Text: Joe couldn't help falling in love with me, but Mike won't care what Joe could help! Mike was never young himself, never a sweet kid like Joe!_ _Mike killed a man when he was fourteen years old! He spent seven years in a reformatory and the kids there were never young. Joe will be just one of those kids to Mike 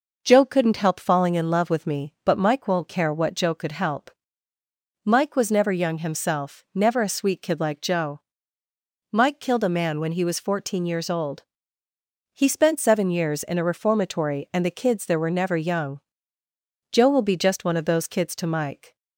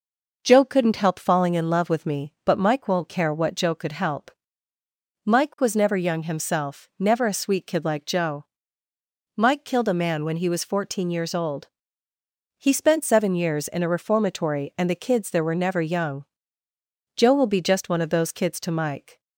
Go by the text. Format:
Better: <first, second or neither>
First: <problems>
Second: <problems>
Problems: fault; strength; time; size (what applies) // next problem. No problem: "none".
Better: neither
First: none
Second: none